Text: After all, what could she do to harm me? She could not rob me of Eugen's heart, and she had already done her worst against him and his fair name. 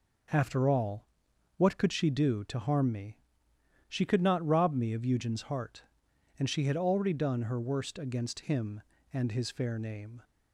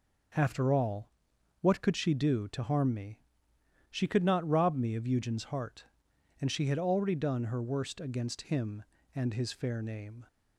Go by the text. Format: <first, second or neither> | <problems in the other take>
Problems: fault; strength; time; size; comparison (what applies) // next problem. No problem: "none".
neither | none